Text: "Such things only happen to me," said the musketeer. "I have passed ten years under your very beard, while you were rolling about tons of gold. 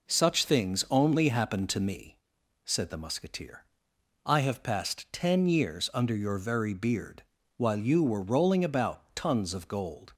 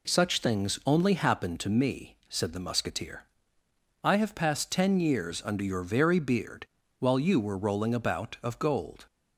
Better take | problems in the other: first | skips "tons"; at 8.3 s

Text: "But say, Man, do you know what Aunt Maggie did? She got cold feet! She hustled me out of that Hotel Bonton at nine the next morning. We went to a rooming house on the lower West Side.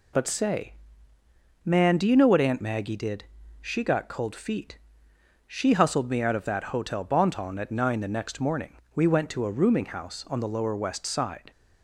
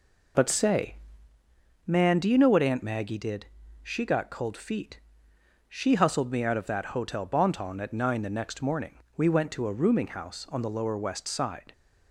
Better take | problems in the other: first | starts louder than the rest; noticeable; until 1.3 s; 4 dB

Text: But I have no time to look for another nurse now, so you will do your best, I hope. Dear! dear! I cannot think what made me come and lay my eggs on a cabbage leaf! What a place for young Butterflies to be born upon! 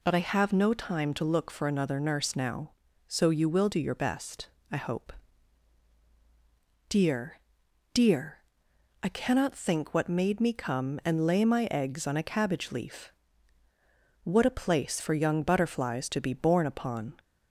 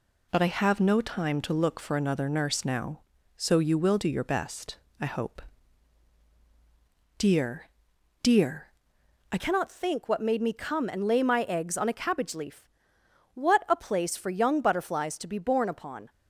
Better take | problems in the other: first | changes voice at "cannot"; from 9.3 s on; 6.7 s long

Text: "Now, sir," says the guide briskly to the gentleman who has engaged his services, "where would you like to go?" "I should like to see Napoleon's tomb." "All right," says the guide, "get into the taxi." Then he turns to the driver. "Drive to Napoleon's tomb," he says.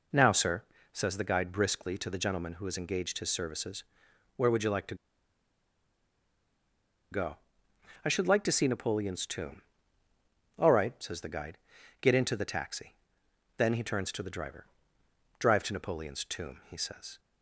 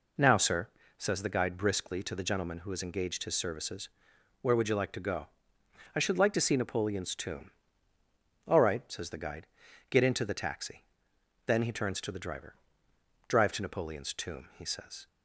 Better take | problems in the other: second | pauses between "to" and "go"; strong; at 4.9 s; 2.1 s long

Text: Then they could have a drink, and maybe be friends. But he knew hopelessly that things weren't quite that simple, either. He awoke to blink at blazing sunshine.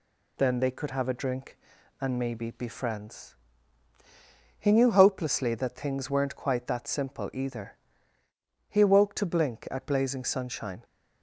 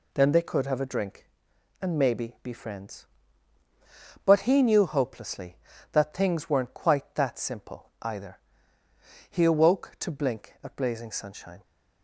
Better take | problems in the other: second | skips "But"; at 3.9 s

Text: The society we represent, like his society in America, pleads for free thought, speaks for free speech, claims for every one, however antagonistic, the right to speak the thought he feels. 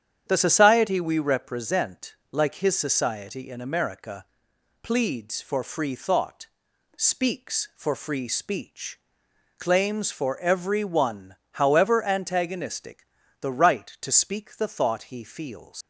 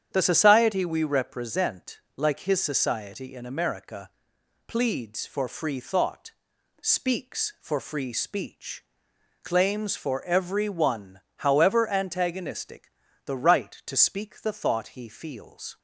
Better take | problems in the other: second | starts louder than the rest; strong; until 1.2 s; 9 dB; strong in the second // leaves "feels" unfinished; at 15.8 s; 125 ms

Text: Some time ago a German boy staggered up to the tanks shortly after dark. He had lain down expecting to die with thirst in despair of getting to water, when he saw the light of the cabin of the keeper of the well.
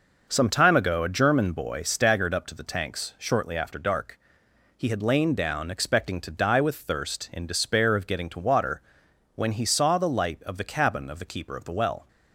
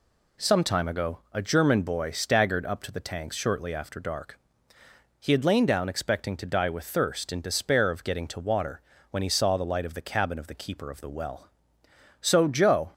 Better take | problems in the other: first | goes on to say "So Joe"; noticeable; from 12.2 s on; 0.72 s long

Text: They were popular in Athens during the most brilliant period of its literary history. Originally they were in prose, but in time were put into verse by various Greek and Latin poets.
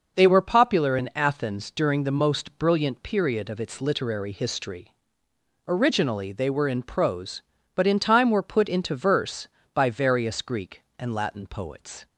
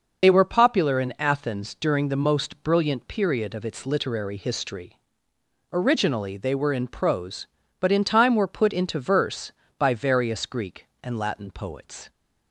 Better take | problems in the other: first | loses the start of "They"; at 0.2 s; 35 ms

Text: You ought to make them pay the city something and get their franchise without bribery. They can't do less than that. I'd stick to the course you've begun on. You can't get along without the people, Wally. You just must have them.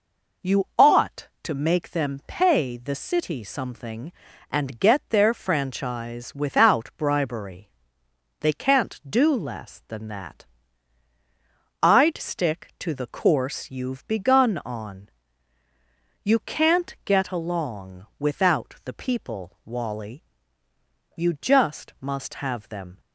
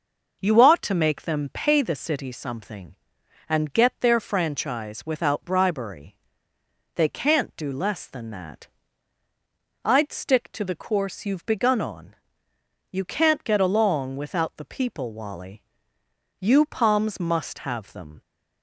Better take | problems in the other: first | says "palms" for "just"; at 16.6 s

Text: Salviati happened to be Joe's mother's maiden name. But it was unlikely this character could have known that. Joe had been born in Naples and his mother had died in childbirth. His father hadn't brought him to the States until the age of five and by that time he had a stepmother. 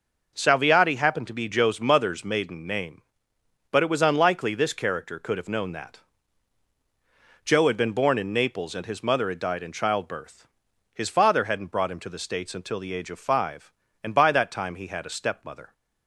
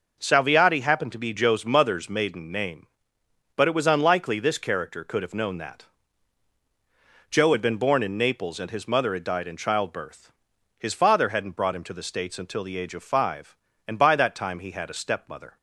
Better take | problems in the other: neither | none

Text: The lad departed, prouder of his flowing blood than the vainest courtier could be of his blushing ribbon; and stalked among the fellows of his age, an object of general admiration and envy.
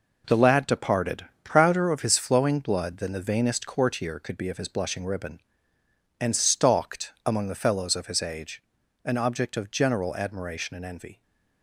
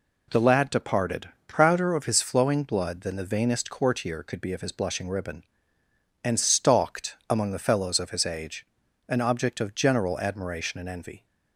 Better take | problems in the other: second | gets quieter; strong; throughout; 8 dB

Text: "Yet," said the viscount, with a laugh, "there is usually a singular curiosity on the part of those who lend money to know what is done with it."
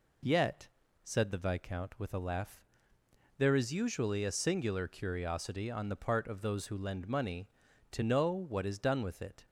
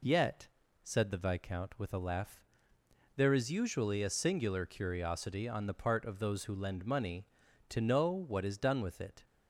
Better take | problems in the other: neither | none

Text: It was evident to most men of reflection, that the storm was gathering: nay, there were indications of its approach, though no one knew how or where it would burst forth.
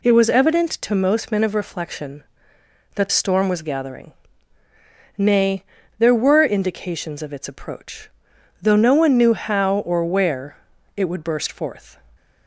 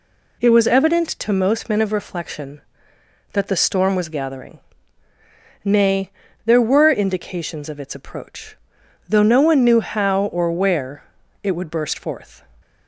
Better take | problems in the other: second | skips "the"; at 3.0 s // pauses between "where" and "it"; at 10.5 s; 0.40 s long; also in the second

